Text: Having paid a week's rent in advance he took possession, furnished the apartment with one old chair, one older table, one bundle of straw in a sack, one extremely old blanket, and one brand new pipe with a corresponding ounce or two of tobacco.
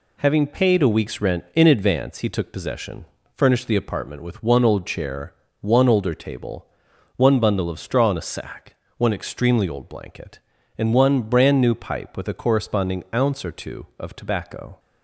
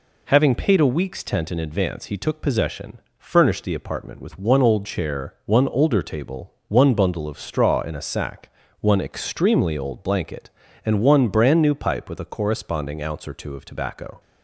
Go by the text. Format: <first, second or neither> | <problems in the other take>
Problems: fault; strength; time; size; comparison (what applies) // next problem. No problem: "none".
first | says "tent" for "rent"; at 1.2 s